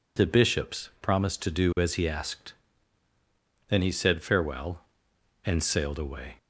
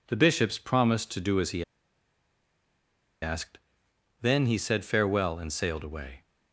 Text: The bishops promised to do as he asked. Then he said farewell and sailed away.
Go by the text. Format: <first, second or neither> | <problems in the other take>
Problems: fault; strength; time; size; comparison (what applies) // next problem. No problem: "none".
first | pauses between "he" and "asked"; strong; at 1.6 s; 1.5 s long